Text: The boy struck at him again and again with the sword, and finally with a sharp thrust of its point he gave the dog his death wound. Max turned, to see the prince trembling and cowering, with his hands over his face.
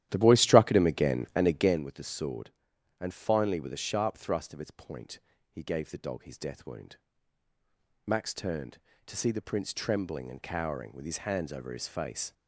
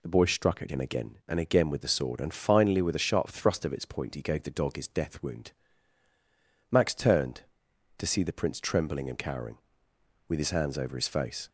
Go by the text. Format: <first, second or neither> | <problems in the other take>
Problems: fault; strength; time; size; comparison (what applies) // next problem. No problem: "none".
second | starts louder than the rest; strong; until 1.8 s; 12.5 dB // pauses between "point" and "he"; slight; at 5.1 s; 0.32 s long